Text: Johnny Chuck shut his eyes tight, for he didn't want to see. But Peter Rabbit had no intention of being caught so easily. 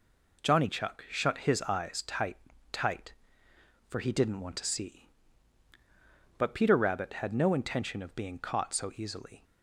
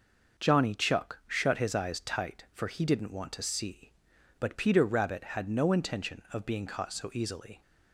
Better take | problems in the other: second | says "tight" twice; at 2.7 s

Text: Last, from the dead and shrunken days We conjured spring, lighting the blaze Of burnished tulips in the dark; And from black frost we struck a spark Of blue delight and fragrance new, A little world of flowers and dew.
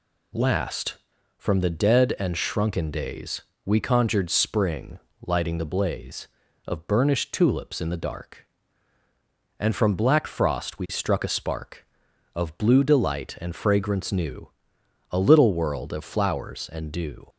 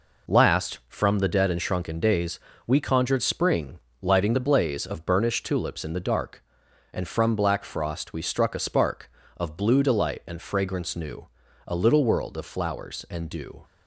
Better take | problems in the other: neither | pauses between "days" and "We"; slight; the same in both

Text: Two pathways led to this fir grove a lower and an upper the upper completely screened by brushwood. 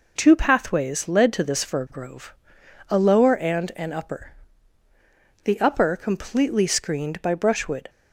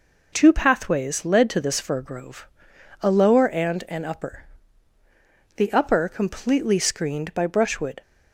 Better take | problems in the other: neither | pauses between "grove" and "a"; noticeable; the same in both // pauses between "upper" and "the"; the same in both

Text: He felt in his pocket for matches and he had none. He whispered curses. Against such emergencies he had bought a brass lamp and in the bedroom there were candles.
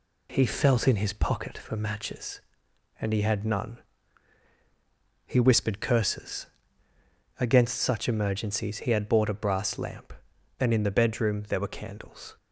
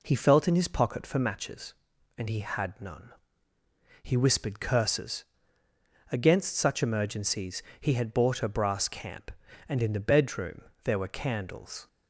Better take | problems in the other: first | pauses between "emergencies" and "he"; slight; at 7.6 s; 0.16 s long // says "camp" for "lamp"; at 8.8 s // pauses between "bedroom" and "there"; slight; at 10.6 s; 0.20 s long

